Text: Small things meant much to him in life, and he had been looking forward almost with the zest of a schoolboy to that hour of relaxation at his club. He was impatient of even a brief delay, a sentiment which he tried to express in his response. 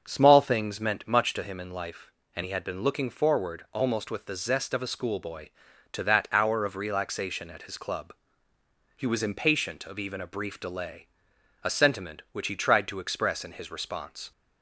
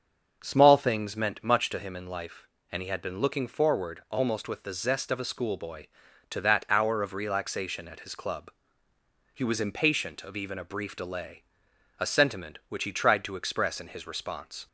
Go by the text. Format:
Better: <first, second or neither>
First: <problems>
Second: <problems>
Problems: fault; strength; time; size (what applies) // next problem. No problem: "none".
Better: neither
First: starts louder than the rest; until 1.0 s; 6.5 dB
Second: starts louder than the rest; until 1.4 s; 6.5 dB